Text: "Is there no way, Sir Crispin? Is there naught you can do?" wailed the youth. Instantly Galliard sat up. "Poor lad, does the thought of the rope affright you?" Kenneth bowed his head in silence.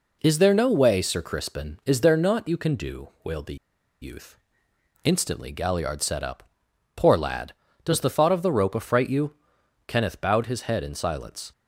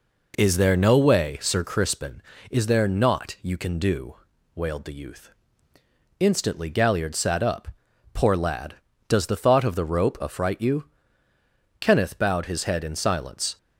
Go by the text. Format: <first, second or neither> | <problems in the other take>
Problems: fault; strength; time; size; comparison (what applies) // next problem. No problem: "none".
second | pauses between "the" and "youth"; at 3.5 s; 0.45 s long